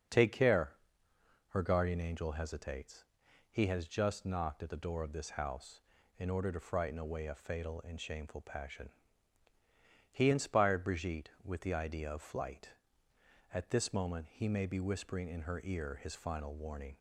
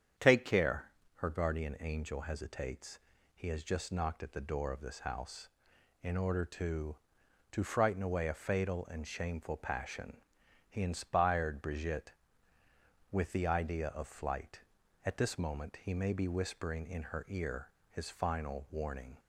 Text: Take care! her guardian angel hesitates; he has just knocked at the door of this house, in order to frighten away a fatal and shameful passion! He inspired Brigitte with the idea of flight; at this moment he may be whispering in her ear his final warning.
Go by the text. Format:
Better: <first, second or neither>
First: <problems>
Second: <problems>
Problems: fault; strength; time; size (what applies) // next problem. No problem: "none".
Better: first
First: starts louder than the rest; until 1.8 s; 6.5 dB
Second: starts louder than the rest; strong; until 1.4 s; 8 dB // says "to" twice; at 7.5 s // pauses between "ear" and "his"; slight; at 17.7 s; 0.18 s long